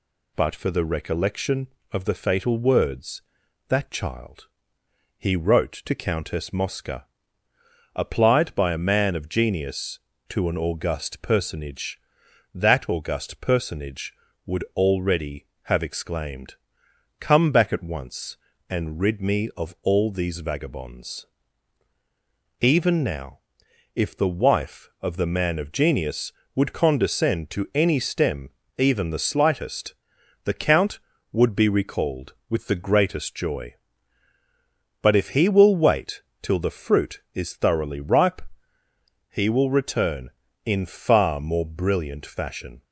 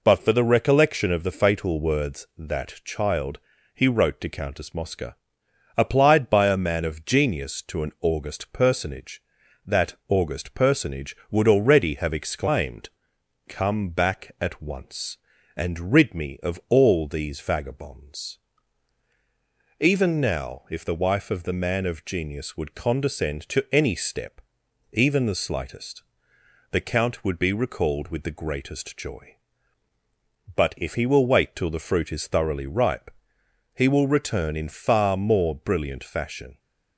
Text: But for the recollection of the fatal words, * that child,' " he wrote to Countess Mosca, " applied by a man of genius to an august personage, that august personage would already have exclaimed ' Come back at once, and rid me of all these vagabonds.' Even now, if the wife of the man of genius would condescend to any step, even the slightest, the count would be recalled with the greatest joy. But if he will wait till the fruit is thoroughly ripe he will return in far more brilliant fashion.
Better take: second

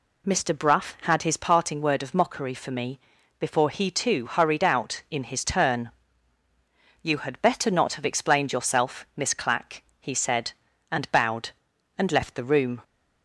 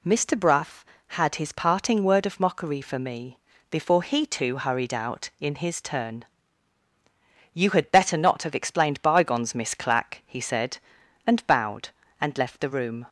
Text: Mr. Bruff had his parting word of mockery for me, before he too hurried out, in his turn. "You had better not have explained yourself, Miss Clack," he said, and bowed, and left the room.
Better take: first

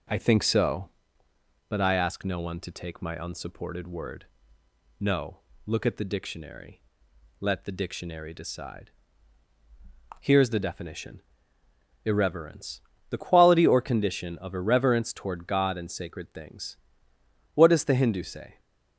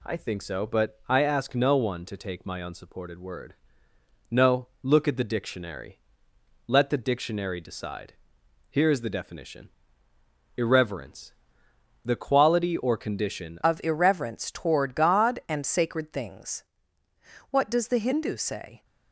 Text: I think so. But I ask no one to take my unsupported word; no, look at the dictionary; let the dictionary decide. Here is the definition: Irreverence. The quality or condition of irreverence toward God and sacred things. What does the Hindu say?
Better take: first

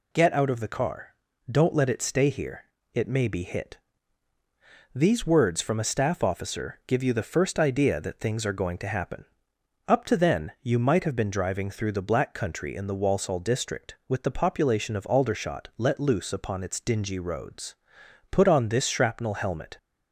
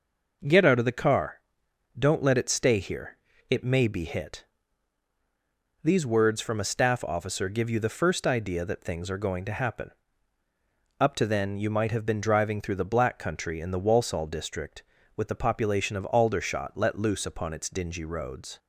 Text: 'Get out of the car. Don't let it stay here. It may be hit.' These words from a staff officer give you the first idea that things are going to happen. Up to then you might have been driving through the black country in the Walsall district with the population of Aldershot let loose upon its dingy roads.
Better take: second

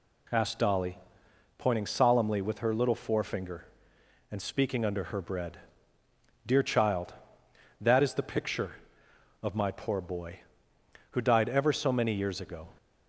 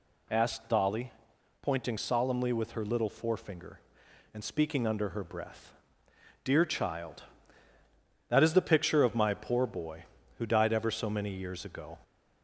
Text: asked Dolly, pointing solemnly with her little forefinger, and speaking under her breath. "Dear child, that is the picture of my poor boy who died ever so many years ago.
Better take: second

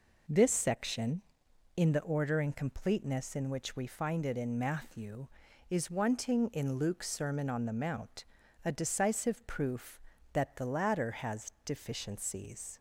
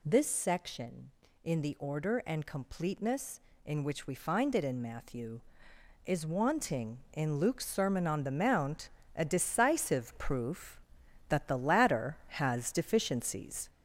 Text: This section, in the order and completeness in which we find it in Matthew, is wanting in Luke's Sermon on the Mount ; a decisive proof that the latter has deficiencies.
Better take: first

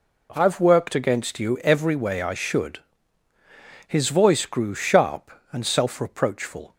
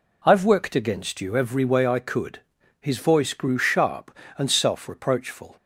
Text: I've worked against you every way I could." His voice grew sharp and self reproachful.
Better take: second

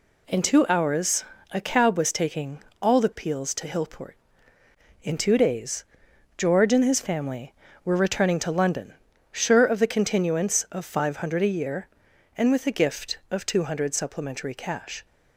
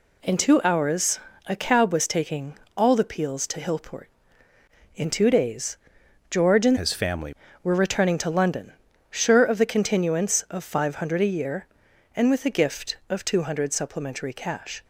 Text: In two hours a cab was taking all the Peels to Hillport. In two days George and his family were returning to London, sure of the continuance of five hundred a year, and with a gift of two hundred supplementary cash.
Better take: first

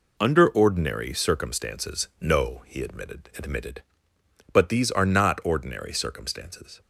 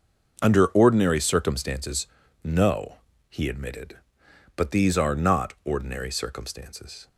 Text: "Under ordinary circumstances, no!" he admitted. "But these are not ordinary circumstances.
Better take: second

